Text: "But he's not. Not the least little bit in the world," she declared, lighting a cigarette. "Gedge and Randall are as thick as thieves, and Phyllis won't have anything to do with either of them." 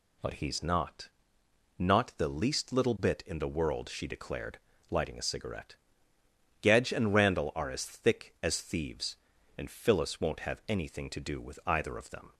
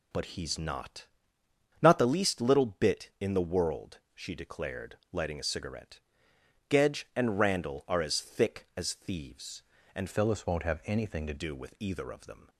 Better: first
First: none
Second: changes voice from "Phyllis" to "to"; from 10.1 to 11.3 s; 1.2 s long

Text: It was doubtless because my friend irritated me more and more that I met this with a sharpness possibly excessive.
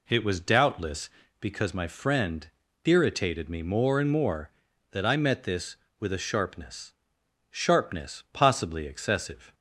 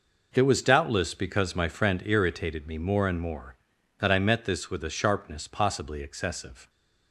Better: second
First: pauses between "friend" and "irritated"; slight; at 2.4 s; 0.36 s long // says "sharpness" twice; at 7.4 s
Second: none

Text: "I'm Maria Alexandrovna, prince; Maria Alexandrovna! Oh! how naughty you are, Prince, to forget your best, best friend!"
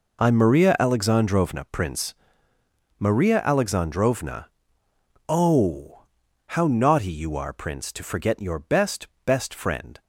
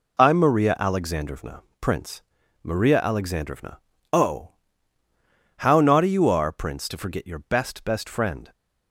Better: neither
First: none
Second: none

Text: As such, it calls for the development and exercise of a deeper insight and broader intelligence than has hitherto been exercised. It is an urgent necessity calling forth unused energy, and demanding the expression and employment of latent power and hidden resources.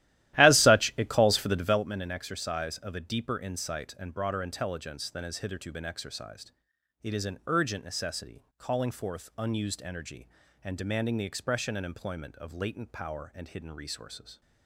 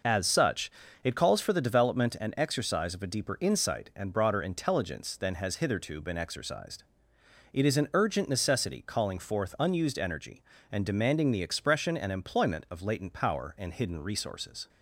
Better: second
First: starts louder than the rest; strong; until 1.9 s; 14.5 dB // pauses between "necessity" and "calling"; slight; at 8.4 s; 0.16 s long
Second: none

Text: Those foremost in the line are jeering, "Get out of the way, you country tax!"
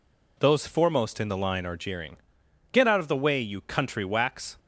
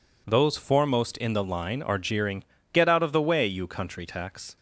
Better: second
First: says "wax" for "tax"; at 4.0 s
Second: none

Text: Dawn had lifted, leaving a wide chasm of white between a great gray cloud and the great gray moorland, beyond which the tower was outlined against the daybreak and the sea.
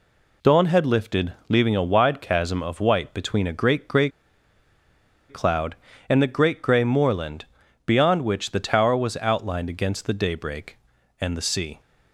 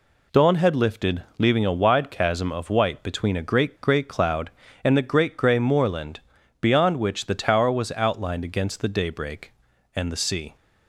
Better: second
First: pauses between "gray" and "cloud"; at 4.0 s; 1.2 s long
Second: none

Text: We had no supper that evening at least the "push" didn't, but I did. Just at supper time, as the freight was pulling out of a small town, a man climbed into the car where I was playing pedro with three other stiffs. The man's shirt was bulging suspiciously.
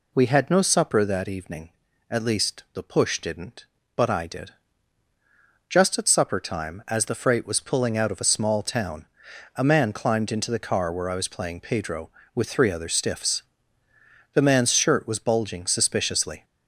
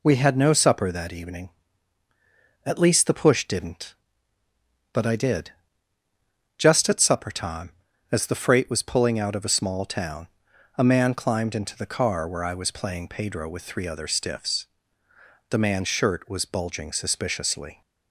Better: neither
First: none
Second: none

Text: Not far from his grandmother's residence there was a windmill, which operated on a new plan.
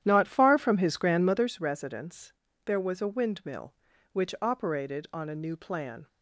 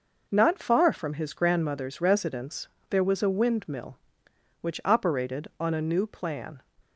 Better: second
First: starts louder than the rest; strong; until 1.5 s; 11 dB // pauses between "residence" and "there"; slight; at 2.3 s; 0.32 s long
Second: pauses between "residence" and "there"; slight; at 2.6 s; 0.22 s long

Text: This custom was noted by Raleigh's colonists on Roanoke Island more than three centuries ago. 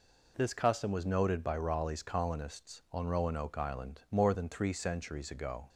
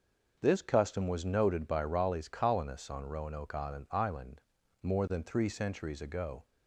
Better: first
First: none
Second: starts louder than the rest; noticeable; until 1.4 s; 6 dB // says "Island" twice; at 3.8 s

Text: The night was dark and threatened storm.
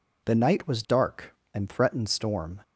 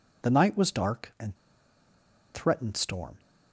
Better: first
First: none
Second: pauses between "and" and "threatened"; at 1.3 s; 0.99 s long

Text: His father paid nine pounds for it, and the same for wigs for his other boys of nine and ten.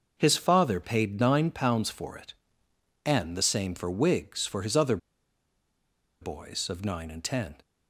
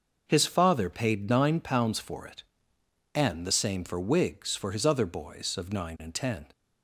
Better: second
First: starts louder than the rest; noticeable; until 1.2 s; 6 dB // pauses between "other" and "boys"; at 4.9 s; 1.2 s long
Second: starts louder than the rest; noticeable; until 1.2 s; 6 dB

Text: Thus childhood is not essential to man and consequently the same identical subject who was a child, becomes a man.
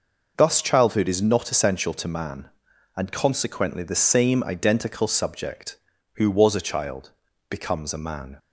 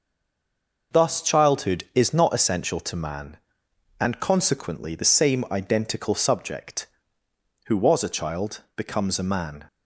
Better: first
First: none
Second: stays silent before the first word; slight; until 0.9 s; 0.9 s long

